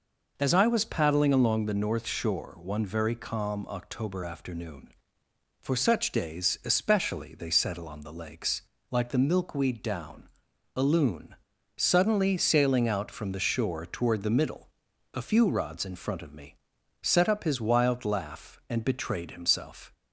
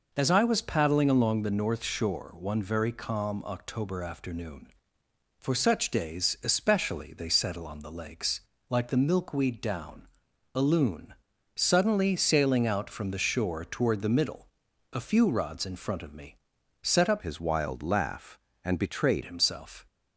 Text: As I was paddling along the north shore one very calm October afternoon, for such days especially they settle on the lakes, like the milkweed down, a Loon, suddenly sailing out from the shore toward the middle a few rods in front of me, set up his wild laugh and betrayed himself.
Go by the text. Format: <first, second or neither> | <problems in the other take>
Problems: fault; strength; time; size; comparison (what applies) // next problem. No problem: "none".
first | pauses between "middle" and "a"; at 14.4 s; 0.44 s long; also in the first // changes voice from "his" to "betrayed"; from 17.2 to 19.2 s; 2.0 s long